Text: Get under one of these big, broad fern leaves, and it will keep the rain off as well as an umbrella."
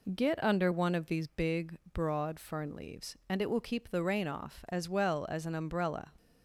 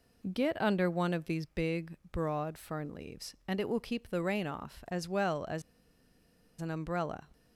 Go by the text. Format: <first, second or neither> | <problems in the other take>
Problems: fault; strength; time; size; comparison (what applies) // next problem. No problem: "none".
first | pauses between "as" and "an"; at 5.6 s; 0.99 s long